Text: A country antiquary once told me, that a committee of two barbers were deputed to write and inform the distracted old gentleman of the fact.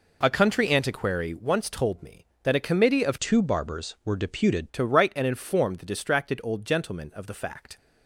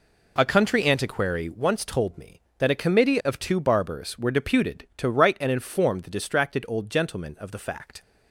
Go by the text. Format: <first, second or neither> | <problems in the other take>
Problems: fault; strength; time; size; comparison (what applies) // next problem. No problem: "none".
second | changes voice from "two" to "deputed"; from 3.2 to 4.6 s; 1.4 s long